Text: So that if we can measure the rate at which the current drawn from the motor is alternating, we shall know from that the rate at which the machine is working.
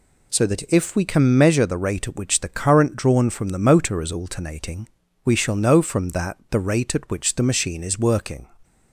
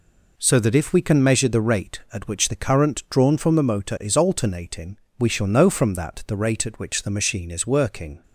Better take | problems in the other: neither | none

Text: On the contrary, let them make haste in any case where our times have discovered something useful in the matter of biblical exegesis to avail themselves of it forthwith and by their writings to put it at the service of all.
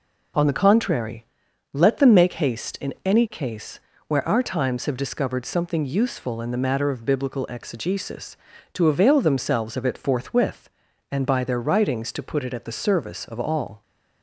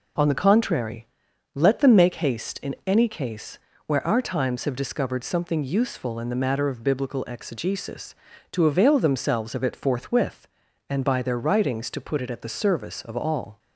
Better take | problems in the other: neither | pauses between "case" and "where"; slight; the same in both

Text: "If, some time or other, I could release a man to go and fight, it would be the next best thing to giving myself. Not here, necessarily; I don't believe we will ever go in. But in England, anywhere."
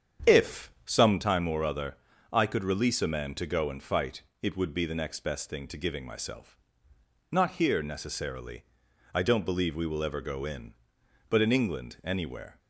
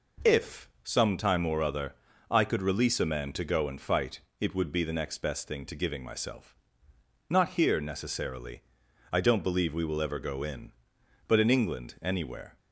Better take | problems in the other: second | starts louder than the rest; strong; until 1.4 s; 8 dB

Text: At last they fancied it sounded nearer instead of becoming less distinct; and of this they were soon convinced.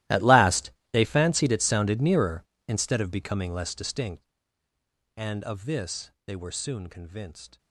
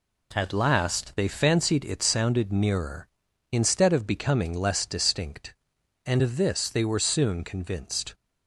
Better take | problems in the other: second | gets quieter; strong; throughout; 20.5 dB // pauses between "last" and "they"; slight; at 0.7 s; 0.22 s long // pauses between "this" and "they"; slight; at 6.1 s; 0.16 s long

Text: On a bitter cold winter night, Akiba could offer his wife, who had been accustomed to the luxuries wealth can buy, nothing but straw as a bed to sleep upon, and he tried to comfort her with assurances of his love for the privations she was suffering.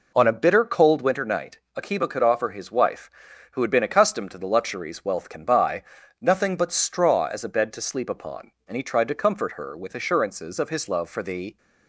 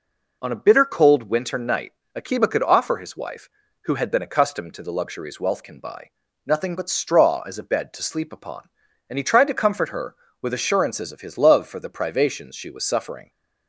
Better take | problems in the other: second | stops before "privations she was suffering"; at 11.5 s

